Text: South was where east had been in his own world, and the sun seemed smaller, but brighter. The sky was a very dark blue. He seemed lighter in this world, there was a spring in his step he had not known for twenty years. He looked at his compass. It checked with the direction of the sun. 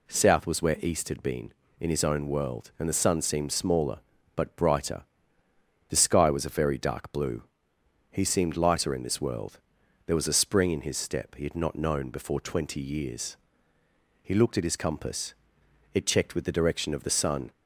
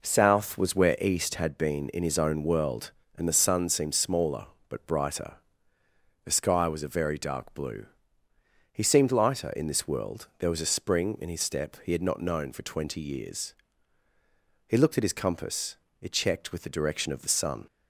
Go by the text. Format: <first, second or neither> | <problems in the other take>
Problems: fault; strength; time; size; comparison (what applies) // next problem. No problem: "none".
second | says "before" for "for"; at 12.1 s